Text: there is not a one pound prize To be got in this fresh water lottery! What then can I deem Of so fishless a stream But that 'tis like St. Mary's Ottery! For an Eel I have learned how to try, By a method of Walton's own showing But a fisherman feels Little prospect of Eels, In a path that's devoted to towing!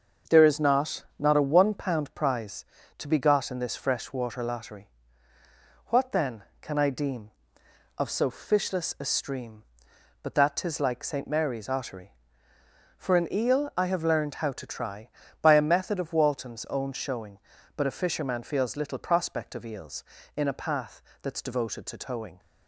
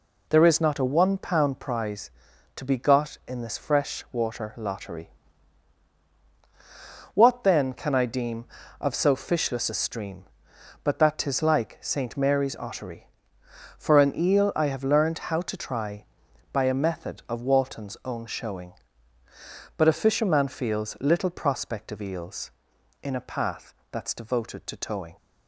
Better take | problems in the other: second | starts louder than the rest; until 1.4 s; 6.5 dB // says "not" twice; at 1.1 s // pauses between "path" and "that's"; slight; at 21.0 s; 0.20 s long; slight in the second

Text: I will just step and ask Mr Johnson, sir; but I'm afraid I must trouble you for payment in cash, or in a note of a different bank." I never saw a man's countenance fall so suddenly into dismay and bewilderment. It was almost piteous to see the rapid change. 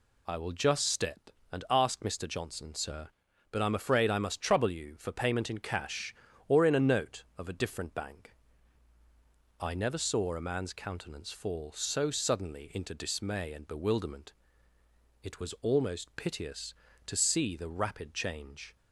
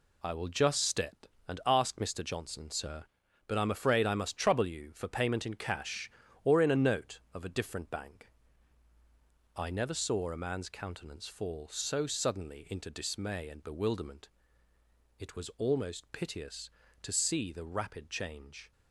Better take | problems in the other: first | gets quieter; strong; throughout; 7.5 dB

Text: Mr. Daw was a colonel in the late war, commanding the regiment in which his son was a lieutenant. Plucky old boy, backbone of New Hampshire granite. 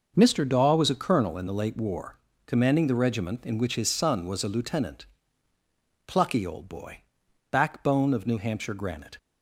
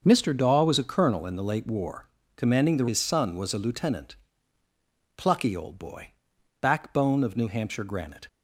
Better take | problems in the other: first | starts louder than the rest; until 1.0 s; 6.5 dB // skips "regiment in which"; at 2.8 s

